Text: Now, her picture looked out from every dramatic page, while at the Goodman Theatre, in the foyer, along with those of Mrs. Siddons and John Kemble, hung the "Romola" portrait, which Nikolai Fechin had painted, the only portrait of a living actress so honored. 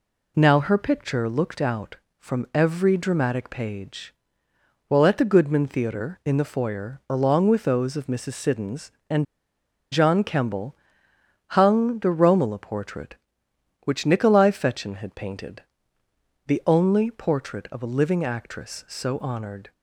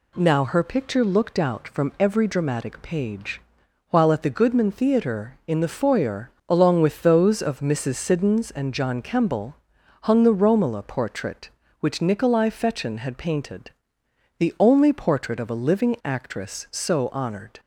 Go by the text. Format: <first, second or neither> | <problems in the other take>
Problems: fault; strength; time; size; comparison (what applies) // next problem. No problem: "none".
second | pauses between "and" and "John"; noticeable; at 9.2 s; 0.67 s long